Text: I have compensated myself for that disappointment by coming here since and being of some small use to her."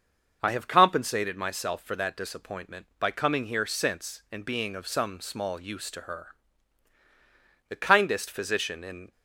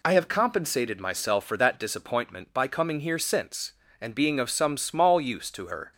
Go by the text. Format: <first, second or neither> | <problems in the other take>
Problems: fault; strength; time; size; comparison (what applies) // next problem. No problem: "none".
second | starts louder than the rest; noticeable; until 1.4 s; 6 dB // goes on to say "The kindest physician in"; from 7.5 s on; 1.5 s long